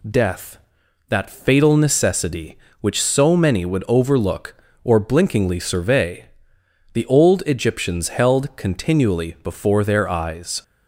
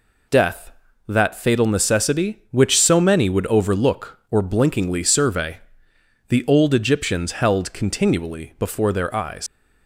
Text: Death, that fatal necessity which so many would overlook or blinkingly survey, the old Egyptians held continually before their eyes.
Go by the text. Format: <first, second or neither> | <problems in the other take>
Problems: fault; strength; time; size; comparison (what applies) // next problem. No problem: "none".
first | leaves "eyes" unfinished; at 9.4 s; 95 ms